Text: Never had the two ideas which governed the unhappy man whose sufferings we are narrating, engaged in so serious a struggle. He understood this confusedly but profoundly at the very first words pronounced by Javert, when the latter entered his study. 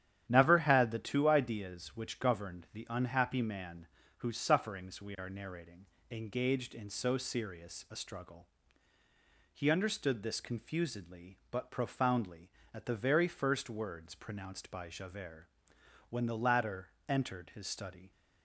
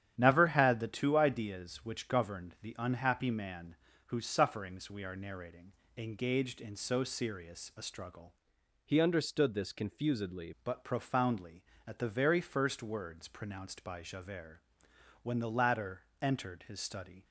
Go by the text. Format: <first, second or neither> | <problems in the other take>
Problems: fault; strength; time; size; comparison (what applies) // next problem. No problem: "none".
first | starts louder than the rest; strong; until 1.1 s; 9.5 dB; strong in the first // pauses between "man" and "whose"; slight; at 3.7 s; 0.32 s long; slight in the first // changes voice from "He" to "confusedly"; from 8.8 to 10.5 s; 1.7 s long // pauses between "latter" and "entered"; slight; at 16.0 s; 0.18 s long; slight in the first